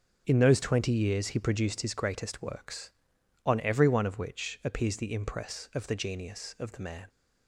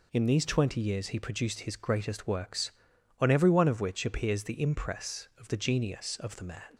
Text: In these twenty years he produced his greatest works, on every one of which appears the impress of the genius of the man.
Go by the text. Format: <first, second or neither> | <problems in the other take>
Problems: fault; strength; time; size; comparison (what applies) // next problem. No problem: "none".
second | says "those" for "these"; at 0.3 s